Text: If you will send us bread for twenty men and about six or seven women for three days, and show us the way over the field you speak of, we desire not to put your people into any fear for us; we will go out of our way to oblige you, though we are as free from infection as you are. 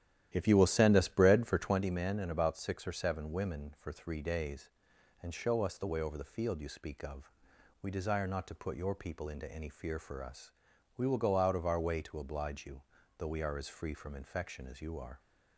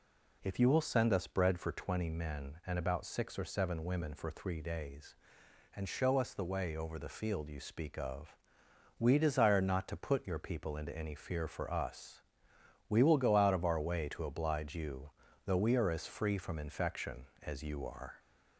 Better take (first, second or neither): second